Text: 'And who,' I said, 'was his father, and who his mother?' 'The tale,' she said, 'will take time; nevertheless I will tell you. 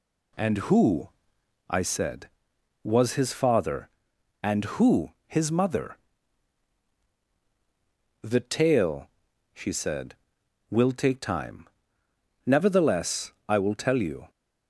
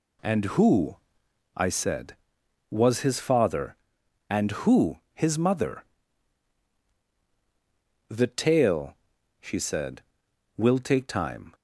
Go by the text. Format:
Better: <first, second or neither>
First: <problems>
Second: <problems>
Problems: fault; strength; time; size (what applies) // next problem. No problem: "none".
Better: first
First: pauses between "who" and "his"; slight; at 5.1 s; 0.16 s long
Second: pauses between "who" and "his"; slight; at 4.9 s; 0.16 s long // stops before "nevertheless I will tell you"; at 11.5 s